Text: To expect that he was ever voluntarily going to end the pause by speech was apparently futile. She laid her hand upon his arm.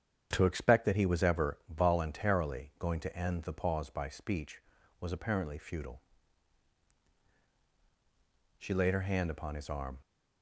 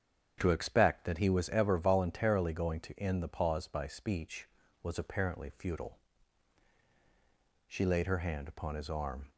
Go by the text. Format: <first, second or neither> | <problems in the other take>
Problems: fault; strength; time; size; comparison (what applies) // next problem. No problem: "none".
neither | starts louder than the rest; strong; the same in both